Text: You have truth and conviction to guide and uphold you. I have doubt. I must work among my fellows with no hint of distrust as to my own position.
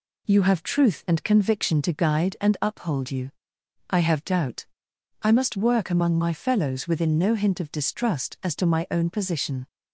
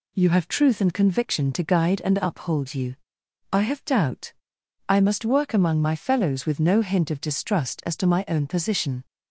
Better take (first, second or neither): second